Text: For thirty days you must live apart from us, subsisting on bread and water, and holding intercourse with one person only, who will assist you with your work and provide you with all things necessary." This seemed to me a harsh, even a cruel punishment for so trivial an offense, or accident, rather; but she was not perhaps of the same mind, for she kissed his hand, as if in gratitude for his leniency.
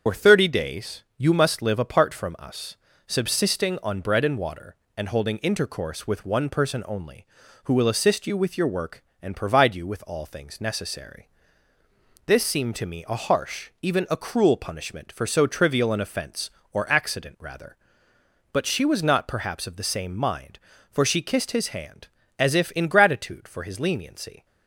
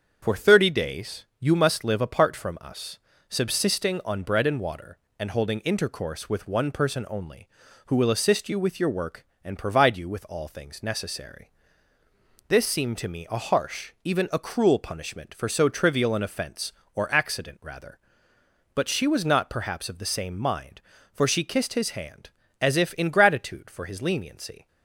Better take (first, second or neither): second